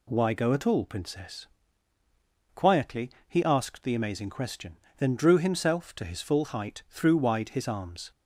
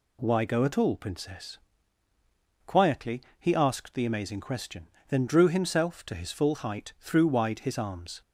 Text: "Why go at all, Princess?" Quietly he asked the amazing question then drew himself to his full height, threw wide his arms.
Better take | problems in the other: neither | pauses between "Quietly" and "he"; slight; the same in both // pauses between "question" and "then"; slight; the same in both

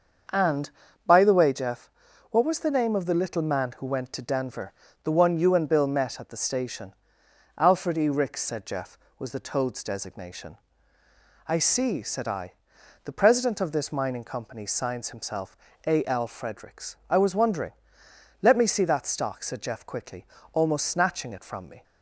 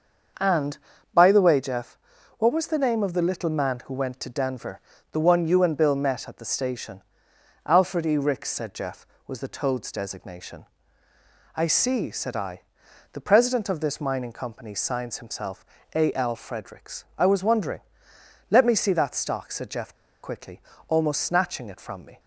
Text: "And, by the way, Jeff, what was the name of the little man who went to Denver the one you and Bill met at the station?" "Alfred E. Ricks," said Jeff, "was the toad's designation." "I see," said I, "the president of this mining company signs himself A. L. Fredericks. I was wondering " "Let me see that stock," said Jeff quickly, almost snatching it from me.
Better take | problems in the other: first | starts louder than the rest; until 1.7 s; 6.5 dB; also in the first // pauses between "Denver" and "the"; slight; at 4.8 s; 0.32 s long; slight in the first // pauses between "himself" and "A"; slight; at 15.6 s; 0.30 s long; slight in the first // pauses between "Jeff" and "quickly"; slight; at 19.9 s; 0.28 s long

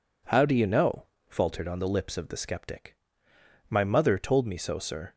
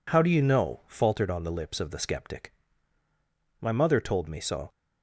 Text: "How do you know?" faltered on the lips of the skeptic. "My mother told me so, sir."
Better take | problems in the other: first | stops before "sir"; at 4.7 s

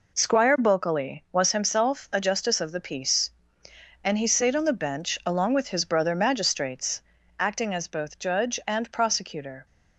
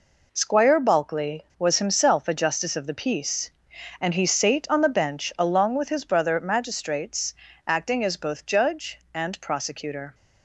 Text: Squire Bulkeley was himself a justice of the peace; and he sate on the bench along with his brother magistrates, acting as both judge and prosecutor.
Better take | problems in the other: neither | none

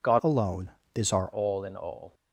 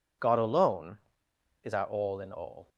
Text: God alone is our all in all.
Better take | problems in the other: second | changes voice from "alone" to "our"; from 0.2 to 1.3 s; 1.1 s long

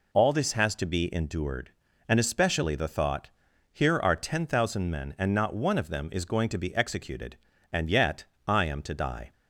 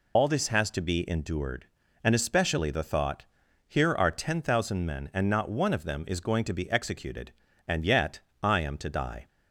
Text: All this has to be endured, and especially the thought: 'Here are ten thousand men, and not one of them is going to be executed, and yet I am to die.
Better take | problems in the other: first | loses the start of "All"; at 0.1 s; 65 ms // pauses between "yet" and "I"; slight; at 8.1 s; 0.24 s long; slight in the first

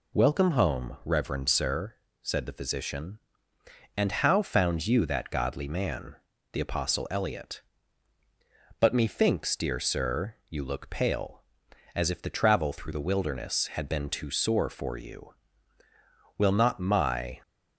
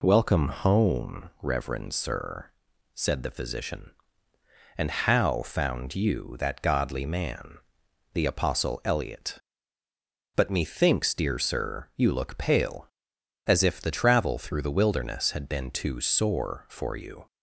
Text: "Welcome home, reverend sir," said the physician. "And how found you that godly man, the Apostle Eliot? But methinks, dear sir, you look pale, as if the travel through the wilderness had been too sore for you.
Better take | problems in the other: second | goes on to say "Will not my"; noticeable; from 16.3 s on; 1.0 s long

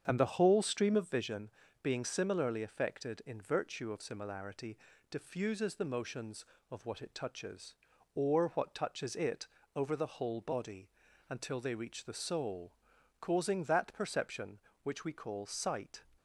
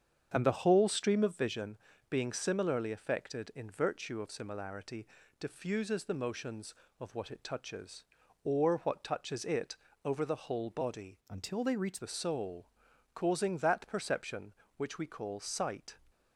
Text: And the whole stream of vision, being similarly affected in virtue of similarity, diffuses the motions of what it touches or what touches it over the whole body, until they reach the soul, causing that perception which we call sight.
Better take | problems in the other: first | starts louder than the rest; strong; until 1.3 s; 7.5 dB; strong in the first // pauses between "it" and "over"; slight; at 9.7 s; 0.28 s long; slight in the first // changes voice from "until" to "reach"; from 11.2 to 11.9 s; 0.7 s long

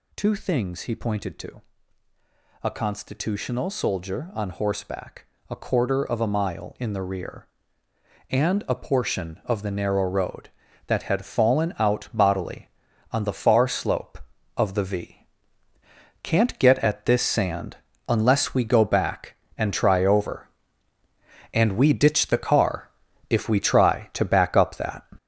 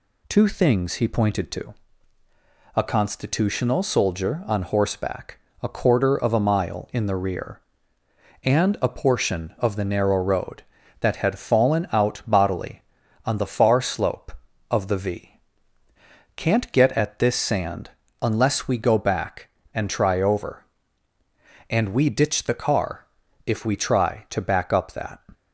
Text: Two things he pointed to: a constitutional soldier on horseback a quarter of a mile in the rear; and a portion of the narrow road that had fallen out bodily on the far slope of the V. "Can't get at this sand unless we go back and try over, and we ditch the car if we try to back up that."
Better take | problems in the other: second | gets louder; throughout; 7 dB // pauses between "horseback" and "a"; slight; at 5.2 s; 0.24 s long; slight in the second // pauses between "sand" and "unless"; slight; at 17.7 s; 0.28 s long; slight in the second // pauses between "car" and "if"; at 22.8 s; 0.40 s long; also in the second

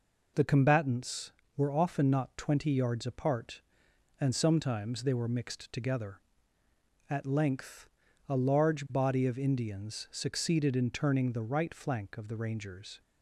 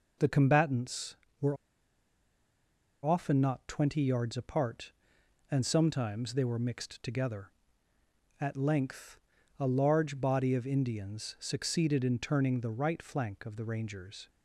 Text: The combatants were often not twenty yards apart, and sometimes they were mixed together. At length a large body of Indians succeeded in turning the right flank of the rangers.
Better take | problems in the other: first | pauses between "were" and "often"; strong; at 1.5 s; 1.4 s long // pauses between "length" and "a"; at 9.1 s; 0.40 s long; also in the first

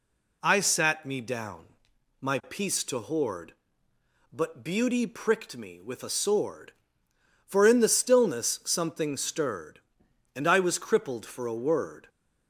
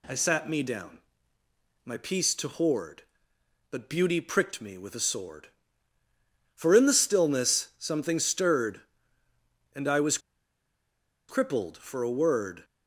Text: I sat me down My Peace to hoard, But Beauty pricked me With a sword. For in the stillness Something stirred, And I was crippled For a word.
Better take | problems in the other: first | pauses between "down" and "My"; noticeable; at 0.9 s; 0.84 s long; noticeable in the first // pauses between "was" and "crippled"; at 10.1 s; 1.1 s long

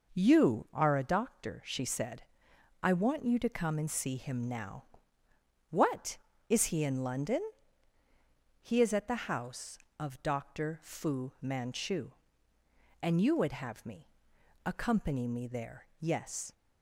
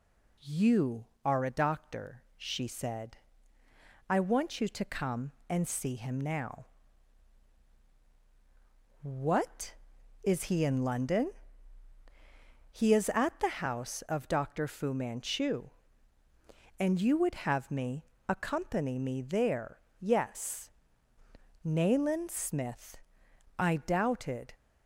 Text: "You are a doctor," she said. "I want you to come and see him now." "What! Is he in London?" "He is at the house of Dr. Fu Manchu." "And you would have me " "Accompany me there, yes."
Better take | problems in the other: first | goes on to say "Nayland Smith I doubted"; strong; from 21.6 s on; 2.9 s long

